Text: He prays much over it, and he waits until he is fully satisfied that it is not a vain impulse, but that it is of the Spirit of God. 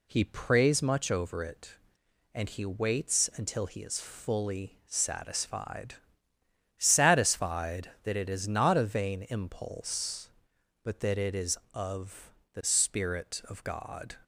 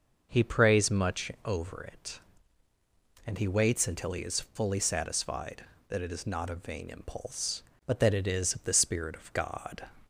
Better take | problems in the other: second | says "satisfied" twice; at 6.7 s // pauses between "of" and "the"; slight; at 12.3 s; 0.22 s long

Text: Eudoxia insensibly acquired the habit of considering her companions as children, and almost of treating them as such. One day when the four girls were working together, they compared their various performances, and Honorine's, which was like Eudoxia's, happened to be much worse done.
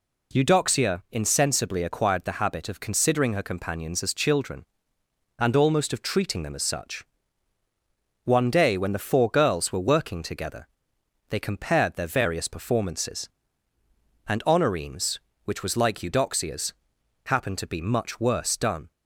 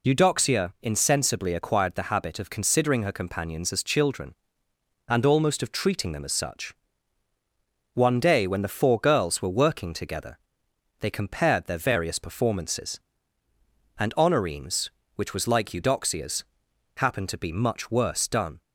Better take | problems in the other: first | loses the start of "Eudoxia"; at 0.0 s; 30 ms

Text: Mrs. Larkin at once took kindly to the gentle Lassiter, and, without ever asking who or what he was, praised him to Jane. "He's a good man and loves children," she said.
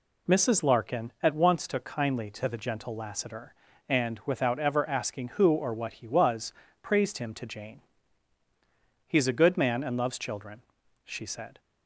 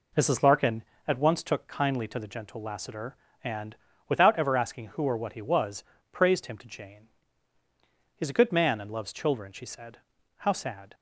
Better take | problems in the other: first | goes on to say "How sad"; from 10.3 s on; 0.56 s long

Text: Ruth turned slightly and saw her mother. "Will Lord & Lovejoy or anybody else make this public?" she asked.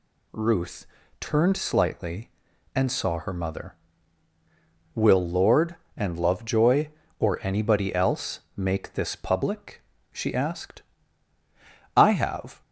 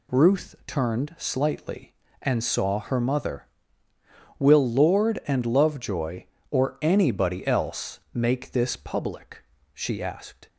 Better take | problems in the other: second | pauses between "Ruth" and "turned"; slight; at 0.8 s; 0.34 s long // goes on to say "I have"; noticeable; from 11.9 s on; 0.66 s long

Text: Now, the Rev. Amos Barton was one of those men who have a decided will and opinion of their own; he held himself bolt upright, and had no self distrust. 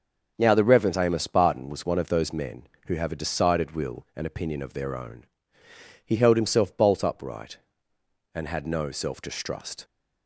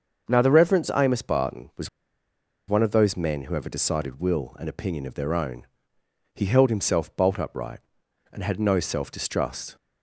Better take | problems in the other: first | starts louder than the rest; until 1.3 s; 6.5 dB; also in the first // pauses between "was" and "one"; noticeable; at 1.8 s; 0.79 s long

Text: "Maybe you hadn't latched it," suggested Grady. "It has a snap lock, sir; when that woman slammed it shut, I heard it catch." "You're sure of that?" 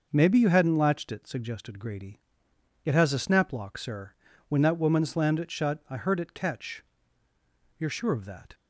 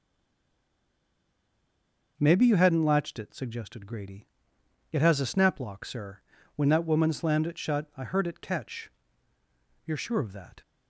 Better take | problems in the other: first | stays silent before the first word; until 2.1 s; 2.1 s long

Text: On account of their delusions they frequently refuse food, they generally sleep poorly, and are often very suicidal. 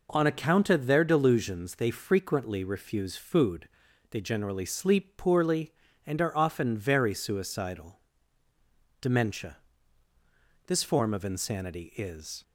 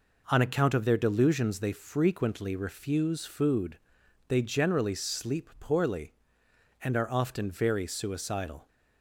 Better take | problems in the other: second | goes on to say "Dementia This form of insanity is"; strong; from 9.0 s on; 3.4 s long

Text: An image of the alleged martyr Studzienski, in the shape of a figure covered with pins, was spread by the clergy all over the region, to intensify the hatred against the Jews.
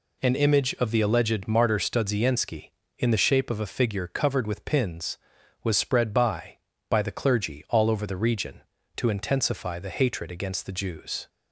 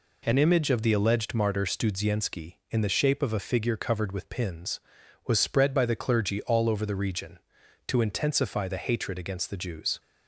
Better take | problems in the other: second | says "by" twice; at 6.9 s

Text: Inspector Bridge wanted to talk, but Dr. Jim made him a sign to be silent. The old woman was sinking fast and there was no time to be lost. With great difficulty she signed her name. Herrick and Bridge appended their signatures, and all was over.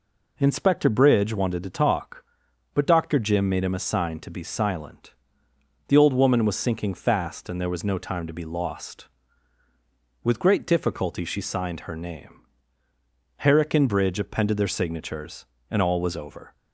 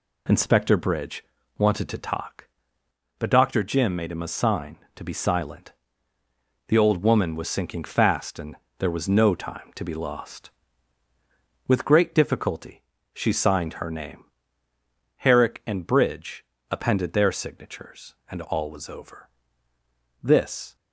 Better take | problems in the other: first | pauses between "Bridge" and "wanted"; slight; at 1.2 s; 0.34 s long // pauses between "and" and "there"; slight; at 8.5 s; 0.22 s long // pauses between "difficulty" and "she"; slight; at 12.8 s; 0.32 s long // pauses between "Bridge" and "appended"; slight; at 16.4 s; 0.28 s long // goes on to say "This"; from 20.2 s on; 0.54 s long

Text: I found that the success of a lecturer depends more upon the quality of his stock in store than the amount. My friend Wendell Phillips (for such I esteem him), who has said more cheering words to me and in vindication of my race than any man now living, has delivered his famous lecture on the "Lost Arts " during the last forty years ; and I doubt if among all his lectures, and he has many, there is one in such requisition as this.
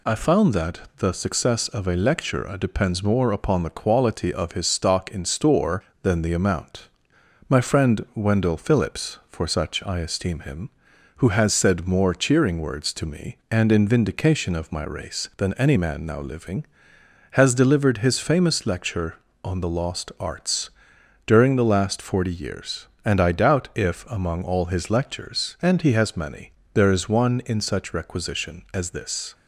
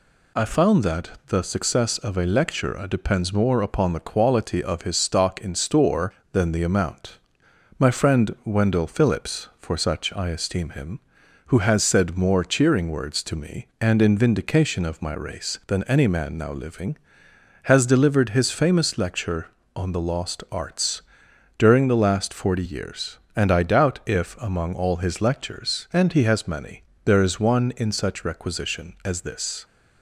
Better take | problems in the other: neither | none

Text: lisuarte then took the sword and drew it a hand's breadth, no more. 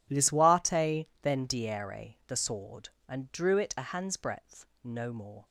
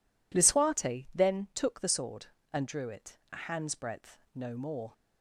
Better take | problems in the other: second | pauses between "lisuarte" and "then"; slight; at 1.0 s; 0.16 s long // says "diere" for "took"; at 1.4 s

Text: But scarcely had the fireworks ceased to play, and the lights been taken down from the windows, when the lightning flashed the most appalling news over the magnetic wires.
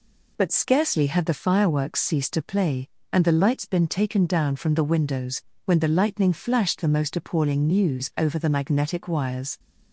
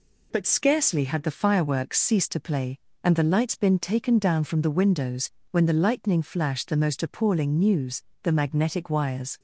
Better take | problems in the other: first | skips "over"; at 8.1 s

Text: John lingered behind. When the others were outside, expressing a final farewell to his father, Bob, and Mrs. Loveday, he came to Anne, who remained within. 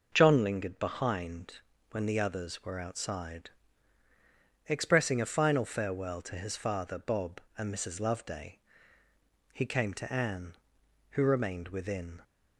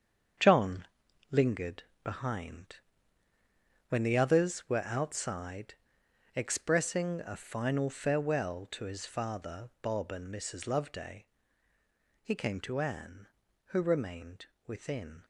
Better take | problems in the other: first | gets quieter; strong; throughout; 8.5 dB // pauses between "John" and "lingered"; noticeable; at 0.8 s; 0.48 s long // pauses between "lingered" and "behind"; slight; at 1.8 s; 0.22 s long // pauses between "remained" and "within"; slight; at 14.4 s; 0.18 s long

